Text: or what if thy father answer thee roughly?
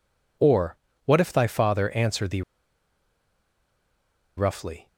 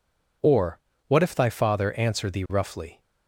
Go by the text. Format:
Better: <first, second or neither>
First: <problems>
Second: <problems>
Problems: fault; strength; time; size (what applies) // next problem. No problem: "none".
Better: second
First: pauses between "or" and "what"; slight; at 0.7 s; 0.30 s long // pauses between "thee" and "roughly"; strong; at 2.4 s; 1.9 s long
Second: pauses between "or" and "what"; slight; at 0.7 s; 0.30 s long